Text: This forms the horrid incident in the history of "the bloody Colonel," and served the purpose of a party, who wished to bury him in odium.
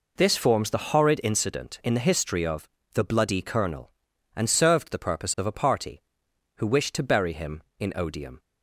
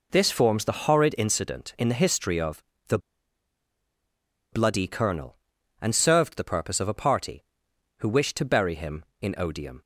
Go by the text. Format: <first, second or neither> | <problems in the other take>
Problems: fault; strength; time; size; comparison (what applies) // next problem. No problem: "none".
first | pauses between "of" and "the"; slight; at 2.6 s; 0.26 s long; slight in the first // pauses between "the" and "bloody"; strong; at 2.9 s; 1.5 s long